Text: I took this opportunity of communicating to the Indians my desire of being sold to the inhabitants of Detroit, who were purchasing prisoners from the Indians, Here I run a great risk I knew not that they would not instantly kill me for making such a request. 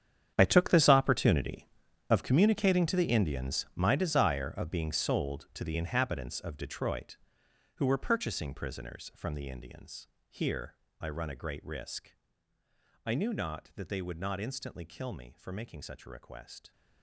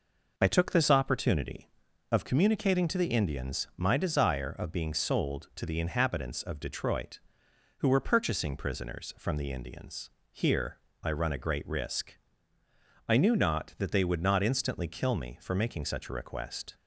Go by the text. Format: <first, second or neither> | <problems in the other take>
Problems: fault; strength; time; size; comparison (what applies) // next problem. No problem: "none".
second | gets quieter; strong; throughout; 15 dB // pauses between "Here" and "I"; slight; at 10.7 s; 0.28 s long; slight in the second // pauses between "risk" and "I"; noticeable; at 12.1 s; 0.90 s long; noticeable in the second